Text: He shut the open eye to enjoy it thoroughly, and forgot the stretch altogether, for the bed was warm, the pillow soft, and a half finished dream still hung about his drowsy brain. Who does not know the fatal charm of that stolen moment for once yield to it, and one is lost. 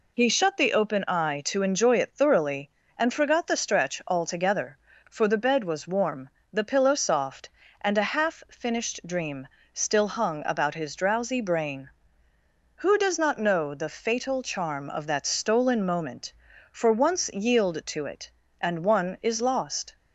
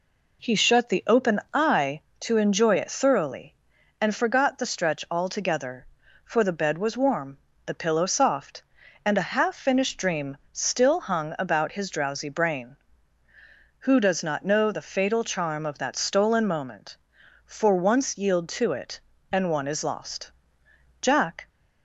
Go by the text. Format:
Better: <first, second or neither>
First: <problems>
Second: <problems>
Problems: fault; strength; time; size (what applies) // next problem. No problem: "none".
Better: first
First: pauses between "dream" and "still"; slight; at 9.4 s; 0.26 s long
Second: pauses between "dream" and "still"; slight; at 10.3 s; 0.16 s long // goes on to say "Jack"; slight; from 21.0 s on; 0.48 s long